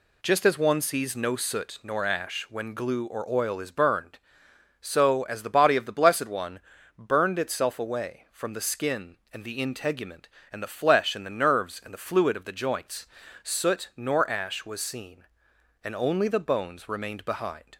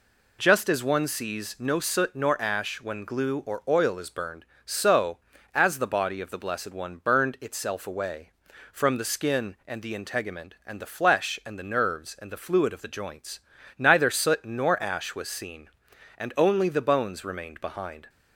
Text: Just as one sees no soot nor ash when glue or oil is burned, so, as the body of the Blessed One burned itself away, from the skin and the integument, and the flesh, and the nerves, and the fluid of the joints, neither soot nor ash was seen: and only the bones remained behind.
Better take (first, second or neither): second